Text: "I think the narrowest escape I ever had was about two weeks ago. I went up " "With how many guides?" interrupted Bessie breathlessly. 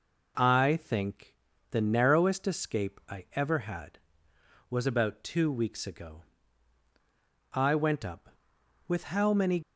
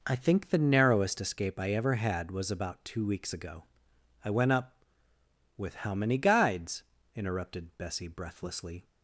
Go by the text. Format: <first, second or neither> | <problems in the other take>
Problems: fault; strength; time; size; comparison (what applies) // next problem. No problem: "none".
second | pauses between "think" and "the"; slight; at 1.3 s; 0.36 s long // stops before "guides interrupted Bessie breathlessly"; at 9.6 s